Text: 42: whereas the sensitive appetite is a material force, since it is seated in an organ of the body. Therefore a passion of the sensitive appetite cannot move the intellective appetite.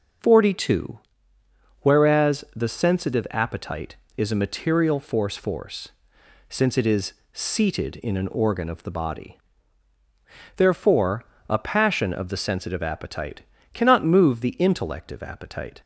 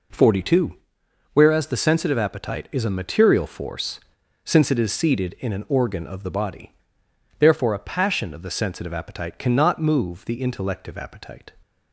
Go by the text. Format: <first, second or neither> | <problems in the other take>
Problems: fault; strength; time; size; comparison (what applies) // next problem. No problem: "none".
second | says "force" twice; at 5.3 s // pauses between "is" and "seated"; slight; at 7.1 s; 0.20 s long // pauses between "Therefore" and "a"; slight; at 11.2 s; 0.24 s long // pauses between "appetite" and "cannot"; slight; at 13.4 s; 0.32 s long